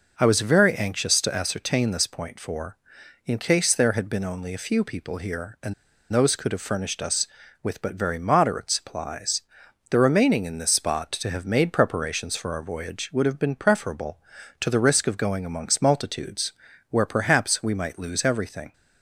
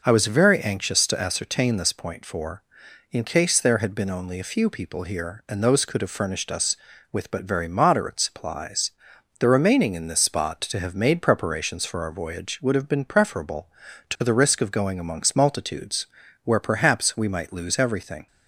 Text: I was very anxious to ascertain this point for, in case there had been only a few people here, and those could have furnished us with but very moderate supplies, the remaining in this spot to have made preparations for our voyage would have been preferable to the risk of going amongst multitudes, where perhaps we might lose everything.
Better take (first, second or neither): second